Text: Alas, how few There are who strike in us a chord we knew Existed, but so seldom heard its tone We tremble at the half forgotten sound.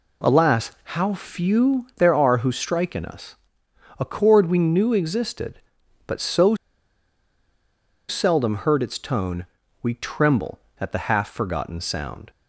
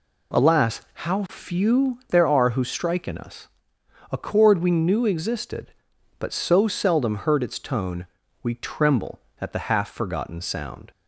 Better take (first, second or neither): second